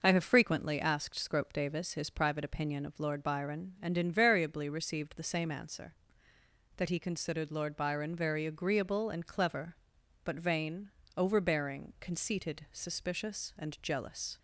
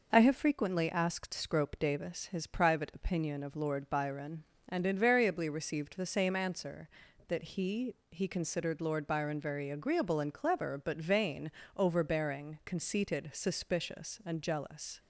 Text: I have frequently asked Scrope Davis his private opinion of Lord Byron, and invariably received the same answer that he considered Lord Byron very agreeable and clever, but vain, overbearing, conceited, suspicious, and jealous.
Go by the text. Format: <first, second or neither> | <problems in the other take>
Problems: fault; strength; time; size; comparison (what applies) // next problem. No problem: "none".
first | says "he" twice; at 8.0 s